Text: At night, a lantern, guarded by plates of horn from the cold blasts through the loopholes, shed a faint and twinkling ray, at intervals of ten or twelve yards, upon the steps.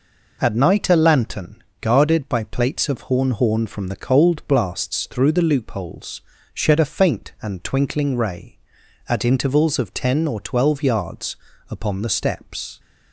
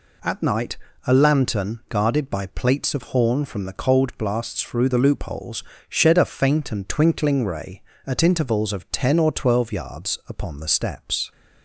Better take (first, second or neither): second